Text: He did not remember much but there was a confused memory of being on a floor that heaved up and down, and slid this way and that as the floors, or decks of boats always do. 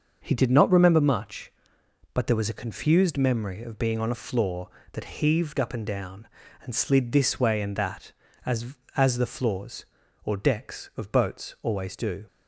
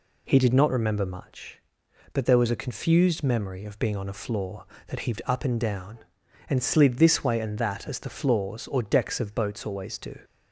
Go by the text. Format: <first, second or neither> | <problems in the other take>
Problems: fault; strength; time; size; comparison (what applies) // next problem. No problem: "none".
second | starts louder than the rest; until 1.2 s; 6.5 dB // says "as" twice; at 8.9 s